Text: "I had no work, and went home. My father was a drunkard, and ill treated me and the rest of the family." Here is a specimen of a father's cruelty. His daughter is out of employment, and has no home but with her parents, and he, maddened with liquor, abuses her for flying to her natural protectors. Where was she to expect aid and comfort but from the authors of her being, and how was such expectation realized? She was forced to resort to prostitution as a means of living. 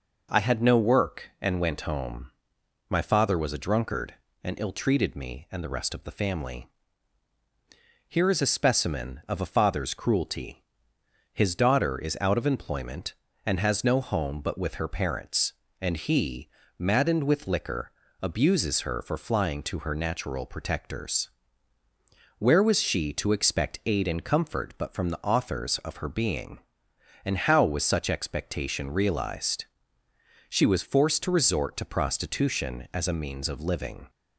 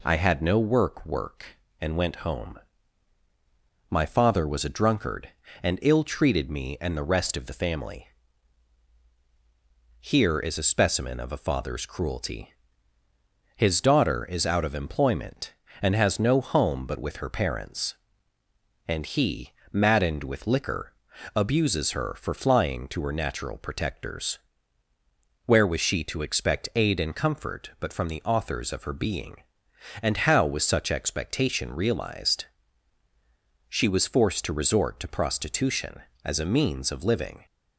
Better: first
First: none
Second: says "work" twice; at 1.0 s

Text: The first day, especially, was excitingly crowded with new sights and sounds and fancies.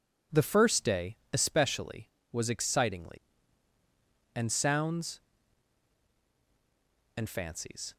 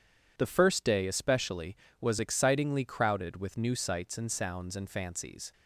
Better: second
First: skips "crowded with new sights"; at 3.7 s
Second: none

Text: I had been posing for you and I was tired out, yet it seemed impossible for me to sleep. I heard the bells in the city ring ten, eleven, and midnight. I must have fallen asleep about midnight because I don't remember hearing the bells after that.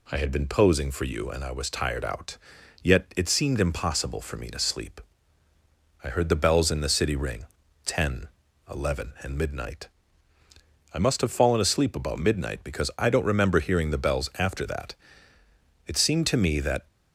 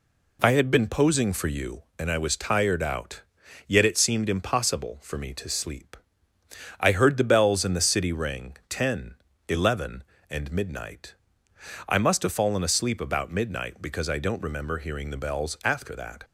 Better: second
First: pauses between "ring" and "ten"; at 7.4 s; 0.40 s long // goes on to say "It seemed to me that"; noticeable; from 15.8 s on; 1.0 s long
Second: none

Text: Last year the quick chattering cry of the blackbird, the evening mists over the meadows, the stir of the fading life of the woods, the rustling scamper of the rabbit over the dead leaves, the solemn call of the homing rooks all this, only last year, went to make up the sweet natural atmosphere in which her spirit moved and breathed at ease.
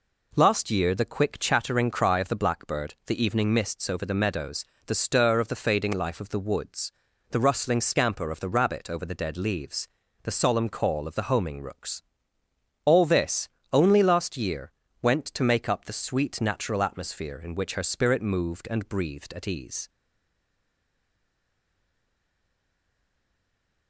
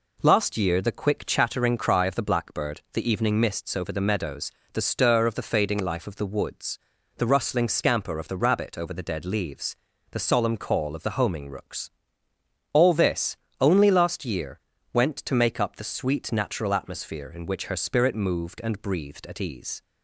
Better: second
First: pauses between "rooks" and "all"; noticeable; at 12.0 s; 0.82 s long // stays silent after the last word; strong; from 19.8 s on; 4.0 s long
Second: pauses between "rooks" and "all"; noticeable; at 11.9 s; 0.82 s long

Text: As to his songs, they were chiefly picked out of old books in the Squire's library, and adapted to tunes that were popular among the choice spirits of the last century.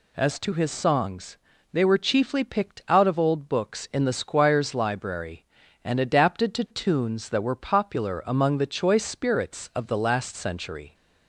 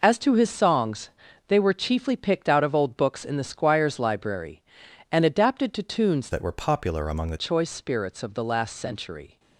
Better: first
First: none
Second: changes voice from "that" to "the"; from 6.3 to 7.3 s; 1.0 s long

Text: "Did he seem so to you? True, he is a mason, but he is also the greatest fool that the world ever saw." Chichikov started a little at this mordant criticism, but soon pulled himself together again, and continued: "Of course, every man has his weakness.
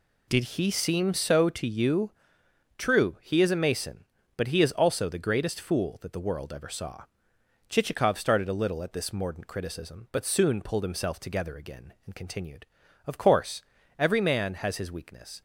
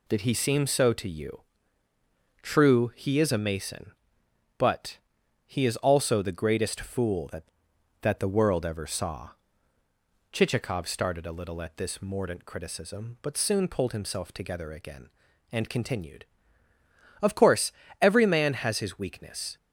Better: first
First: none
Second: pauses between "but" and "he"; noticeable; at 4.9 s; 0.48 s long // says "that" twice; at 8.0 s

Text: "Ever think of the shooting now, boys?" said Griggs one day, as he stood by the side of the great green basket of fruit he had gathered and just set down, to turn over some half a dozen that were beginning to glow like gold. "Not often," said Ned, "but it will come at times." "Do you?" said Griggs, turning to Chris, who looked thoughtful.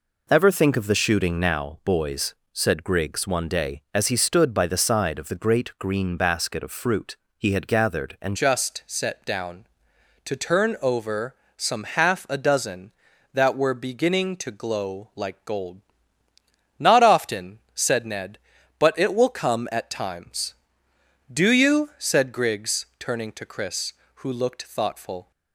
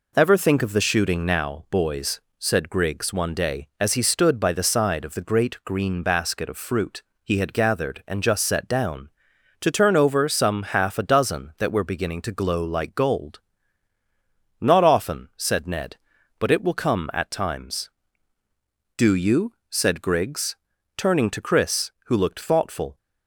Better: second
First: pauses between "fruit" and "he"; slight; at 7.1 s; 0.22 s long // changes voice at "just"; from 8.3 s on; 17.0 s long // pauses between "over" and "some"; slight; at 11.3 s; 0.22 s long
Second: pauses between "fruit" and "he"; slight; at 7.0 s; 0.22 s long

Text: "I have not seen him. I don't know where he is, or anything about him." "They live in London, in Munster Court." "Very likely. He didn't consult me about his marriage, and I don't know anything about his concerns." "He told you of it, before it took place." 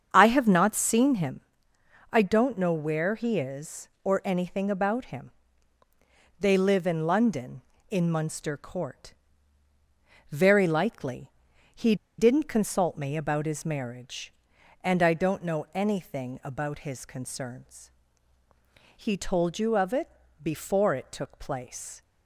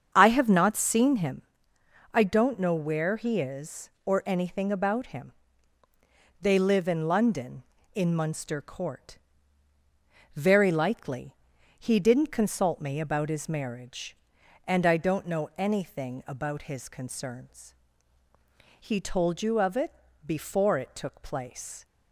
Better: second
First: starts louder than the rest; strong; until 1.1 s; 7.5 dB // pauses between "He" and "didn't"; slight; at 11.9 s; 0.23 s long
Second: starts louder than the rest; strong; until 1.1 s; 7.5 dB

